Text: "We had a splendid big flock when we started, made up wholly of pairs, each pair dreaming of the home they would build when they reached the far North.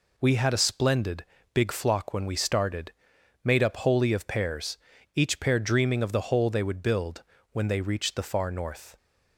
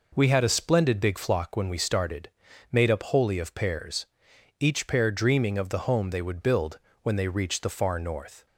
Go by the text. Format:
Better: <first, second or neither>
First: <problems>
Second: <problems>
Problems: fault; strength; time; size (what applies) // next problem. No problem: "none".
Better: second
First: pauses between "splendid" and "big"; slight; at 1.2 s; 0.28 s long // says "hole" for "home"; at 6.3 s // pauses between "build" and "when"; slight; at 7.2 s; 0.30 s long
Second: pauses between "build" and "when"; slight; at 6.7 s; 0.24 s long